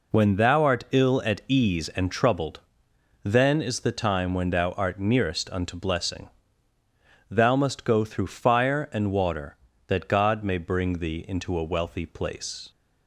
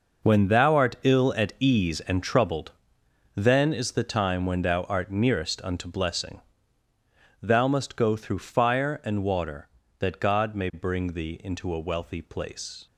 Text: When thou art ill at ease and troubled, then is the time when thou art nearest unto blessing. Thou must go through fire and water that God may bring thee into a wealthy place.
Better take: first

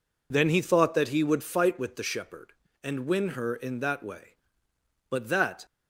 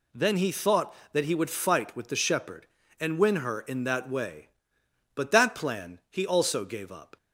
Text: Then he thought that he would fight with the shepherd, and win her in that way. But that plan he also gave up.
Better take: second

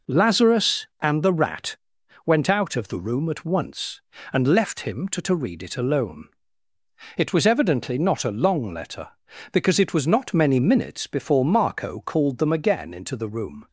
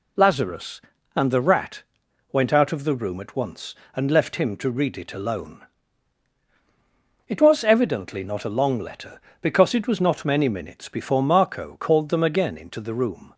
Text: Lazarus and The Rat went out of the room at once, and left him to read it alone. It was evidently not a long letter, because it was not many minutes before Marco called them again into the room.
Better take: second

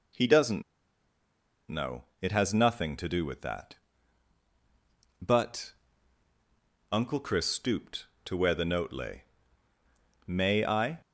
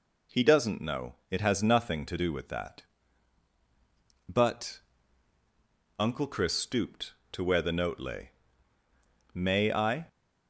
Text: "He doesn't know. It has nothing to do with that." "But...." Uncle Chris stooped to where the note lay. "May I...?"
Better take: second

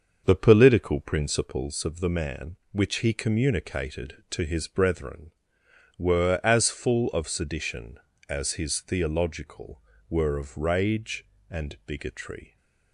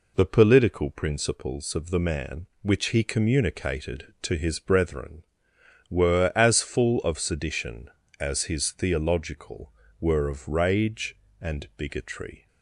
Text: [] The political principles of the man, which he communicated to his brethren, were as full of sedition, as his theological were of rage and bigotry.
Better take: second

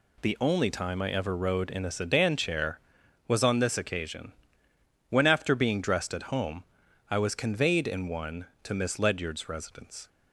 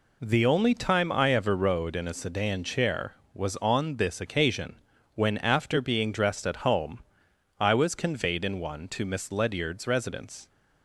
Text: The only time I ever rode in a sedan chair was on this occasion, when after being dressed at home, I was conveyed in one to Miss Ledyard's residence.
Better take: neither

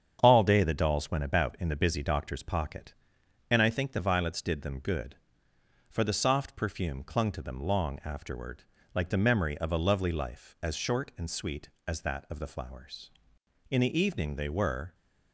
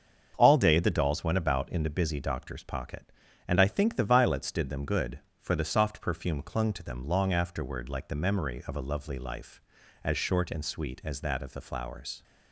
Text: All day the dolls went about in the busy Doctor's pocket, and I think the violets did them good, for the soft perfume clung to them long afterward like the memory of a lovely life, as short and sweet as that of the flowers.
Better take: second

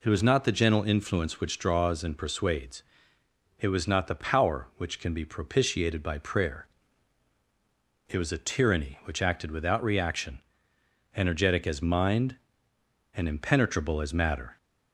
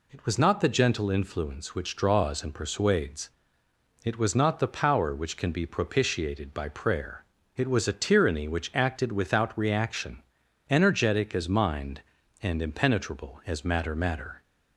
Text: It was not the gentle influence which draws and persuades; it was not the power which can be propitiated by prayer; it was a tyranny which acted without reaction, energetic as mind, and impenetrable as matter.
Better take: first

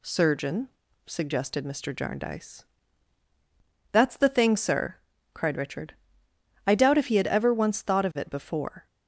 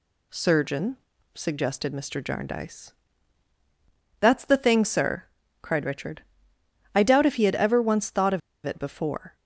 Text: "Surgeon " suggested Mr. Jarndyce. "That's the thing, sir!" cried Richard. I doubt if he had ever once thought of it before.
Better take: first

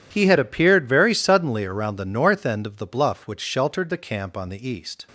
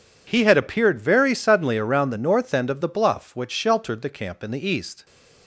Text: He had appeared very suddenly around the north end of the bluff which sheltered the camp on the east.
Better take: first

